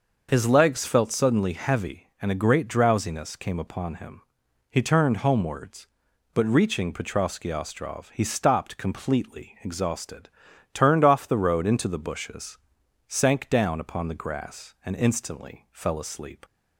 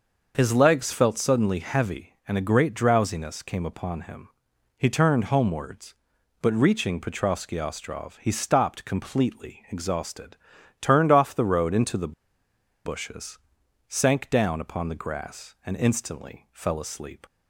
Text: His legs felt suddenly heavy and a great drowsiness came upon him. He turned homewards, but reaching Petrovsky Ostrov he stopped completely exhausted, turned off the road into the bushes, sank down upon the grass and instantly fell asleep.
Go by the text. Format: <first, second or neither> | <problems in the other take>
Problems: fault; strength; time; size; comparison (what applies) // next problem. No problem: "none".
first | starts louder than the rest; noticeable; until 1.3 s; 6 dB; noticeable in the first // pauses between "the" and "bushes"; noticeable; at 12.1 s; 0.73 s long